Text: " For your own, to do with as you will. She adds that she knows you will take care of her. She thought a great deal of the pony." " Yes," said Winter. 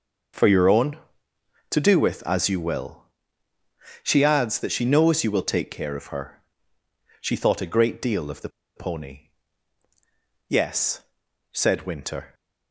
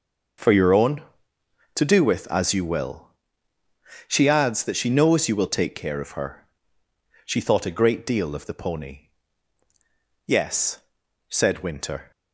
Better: second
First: starts louder than the rest; until 2.0 s; 7 dB // pauses between "the" and "pony"; slight; at 8.4 s; 0.27 s long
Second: starts louder than the rest; until 2.1 s; 7 dB

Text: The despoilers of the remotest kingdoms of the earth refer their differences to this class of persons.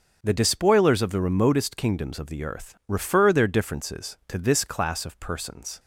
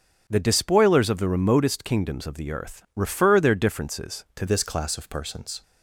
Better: first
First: starts louder than the rest; until 1.2 s; 6.5 dB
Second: starts louder than the rest; until 1.2 s; 7 dB // changes voice at "this"; from 4.4 s on; 1.2 s long

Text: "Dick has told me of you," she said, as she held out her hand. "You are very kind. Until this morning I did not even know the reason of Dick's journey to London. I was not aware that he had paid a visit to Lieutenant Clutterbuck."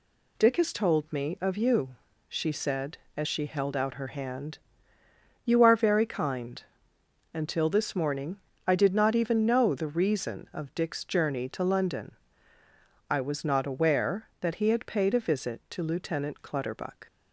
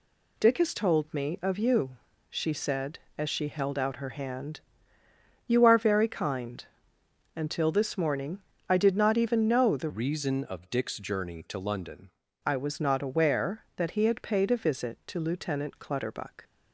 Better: first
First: pauses between "morning" and "I"; slight; at 8.3 s; 0.28 s long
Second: pauses between "morning" and "I"; slight; at 8.4 s; 0.28 s long // changes voice from "reason" to "London"; from 9.8 to 12.1 s; 2.3 s long

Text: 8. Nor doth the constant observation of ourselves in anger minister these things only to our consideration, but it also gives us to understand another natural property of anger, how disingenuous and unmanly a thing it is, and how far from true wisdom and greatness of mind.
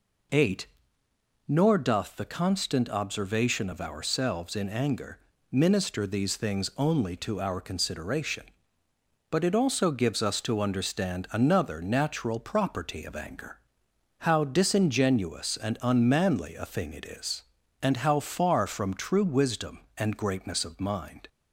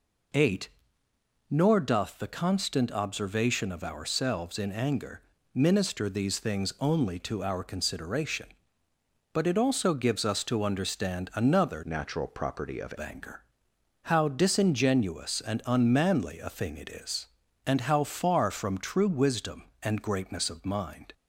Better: first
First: pauses between "anger" and "minister"; slight; at 5.1 s; 0.30 s long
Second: pauses between "anger" and "minister"; slight; at 5.2 s; 0.30 s long // changes voice from "natural" to "of"; from 11.8 to 12.9 s; 1.1 s long

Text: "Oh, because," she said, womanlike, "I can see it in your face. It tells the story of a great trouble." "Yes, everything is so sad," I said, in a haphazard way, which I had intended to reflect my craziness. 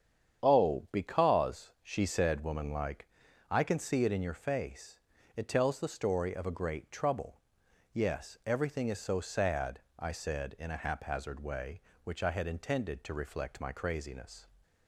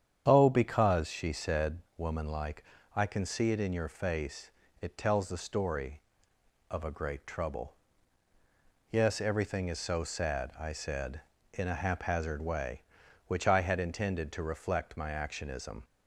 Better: first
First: starts louder than the rest; strong; until 1.4 s; 8.5 dB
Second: starts louder than the rest; strong; until 1.2 s; 8.5 dB // says "actionism" for "craziness"; at 15.1 s

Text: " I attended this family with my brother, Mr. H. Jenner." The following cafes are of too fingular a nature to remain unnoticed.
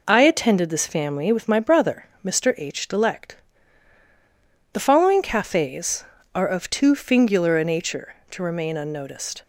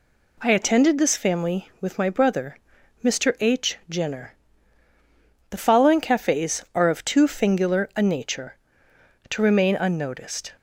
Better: second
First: says "Delect" for "Jenner"; at 2.8 s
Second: none

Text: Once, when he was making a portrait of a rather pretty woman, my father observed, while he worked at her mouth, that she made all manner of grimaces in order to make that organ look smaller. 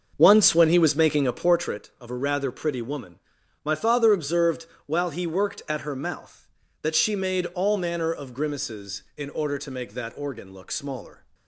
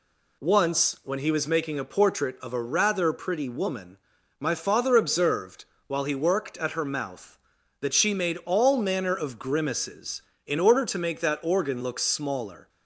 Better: second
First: starts louder than the rest; until 1.6 s; 6.5 dB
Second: none

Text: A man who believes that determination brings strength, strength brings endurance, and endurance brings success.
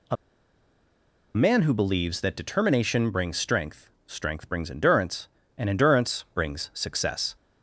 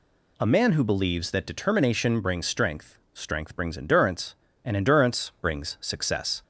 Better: second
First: pauses between "A" and "man"; at 0.1 s; 1.1 s long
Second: none

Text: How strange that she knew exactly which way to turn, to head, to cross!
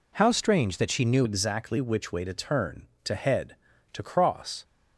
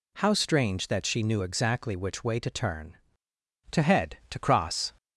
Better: second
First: changes voice at "exactly"; from 1.2 s on; 3.4 s long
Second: none

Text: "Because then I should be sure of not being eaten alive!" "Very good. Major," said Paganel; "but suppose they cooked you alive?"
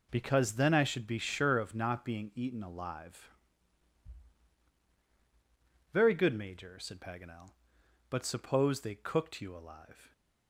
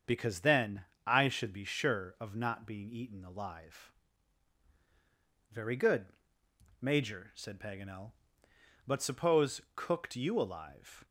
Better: first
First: none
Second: starts louder than the rest; until 1.2 s; 7 dB // pauses between "then" and "I"; slight; at 0.8 s; 0.22 s long // skips "they"; at 9.6 s

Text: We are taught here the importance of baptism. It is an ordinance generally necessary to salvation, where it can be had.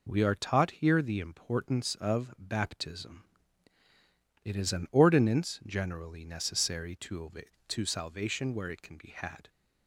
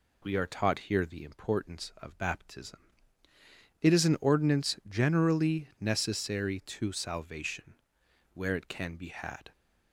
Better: second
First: says "to" twice; at 7.6 s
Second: none

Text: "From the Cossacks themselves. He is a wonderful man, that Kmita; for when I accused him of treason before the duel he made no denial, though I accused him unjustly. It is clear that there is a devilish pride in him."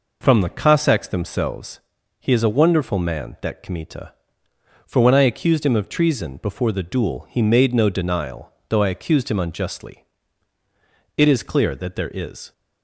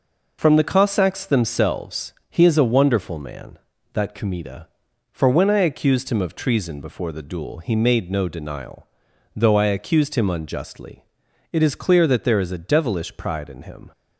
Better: second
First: stops before "a devilish pride in him"; at 12.5 s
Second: none

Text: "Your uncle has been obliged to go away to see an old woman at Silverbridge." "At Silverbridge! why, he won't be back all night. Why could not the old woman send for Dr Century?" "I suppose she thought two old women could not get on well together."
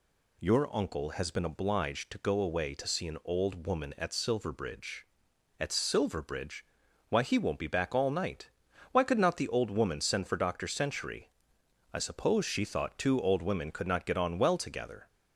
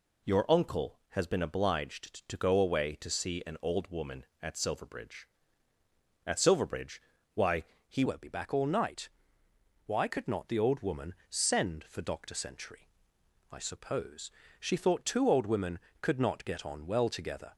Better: first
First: none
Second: changes voice at "won't"; from 8.0 s on; 9.5 s long // pauses between "woman" and "send"; slight; at 11.1 s; 0.16 s long // pauses between "suppose" and "she"; slight; at 14.3 s; 0.30 s long

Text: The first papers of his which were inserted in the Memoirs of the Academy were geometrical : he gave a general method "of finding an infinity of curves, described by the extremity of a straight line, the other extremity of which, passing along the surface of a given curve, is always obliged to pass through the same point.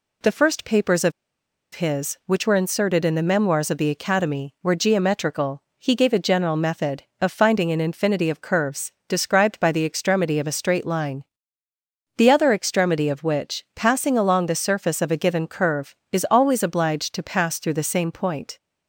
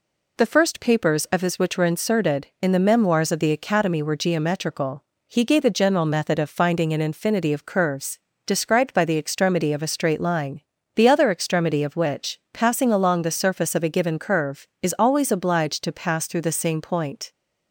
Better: second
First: pauses between "of" and "his"; noticeable; at 1.1 s; 0.63 s long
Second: none

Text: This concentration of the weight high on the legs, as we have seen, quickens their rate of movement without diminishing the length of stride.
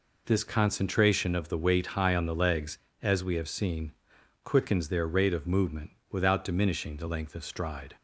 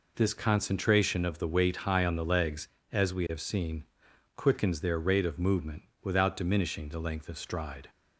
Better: neither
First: pauses between "movement" and "without"; slight; at 5.9 s; 0.20 s long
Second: pauses between "movement" and "without"; slight; at 5.8 s; 0.20 s long

